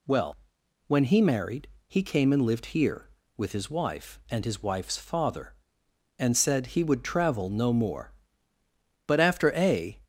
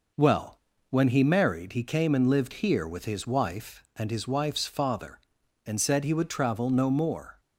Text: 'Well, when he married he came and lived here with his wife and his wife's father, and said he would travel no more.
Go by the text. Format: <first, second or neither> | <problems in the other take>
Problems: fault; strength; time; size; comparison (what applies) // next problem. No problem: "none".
second | pauses between "married" and "he"; slight; at 1.6 s; 0.18 s long // goes on to say "But after a"; noticeable; from 9.0 s on; 0.94 s long